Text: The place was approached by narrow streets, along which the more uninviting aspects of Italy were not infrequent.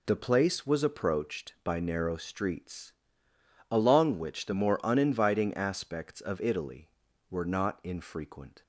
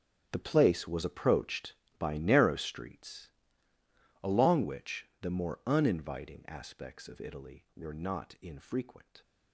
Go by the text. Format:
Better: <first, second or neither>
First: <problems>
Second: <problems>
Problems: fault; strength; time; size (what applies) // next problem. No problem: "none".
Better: first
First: none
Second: gets quieter; strong; throughout; 15 dB